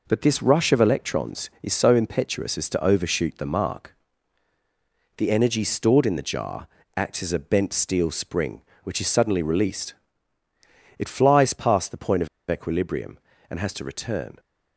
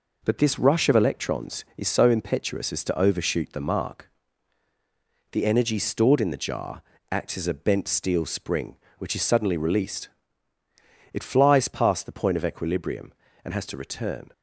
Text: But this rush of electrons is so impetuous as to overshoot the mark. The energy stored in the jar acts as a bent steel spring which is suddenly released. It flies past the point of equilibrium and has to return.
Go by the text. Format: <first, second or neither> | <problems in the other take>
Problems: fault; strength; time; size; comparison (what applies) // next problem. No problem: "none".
second | pauses between "jar" and "acts"; slight; at 6.6 s; 0.28 s long; slight in the second // pauses between "of" and "equilibrium"; slight; at 12.2 s; 0.22 s long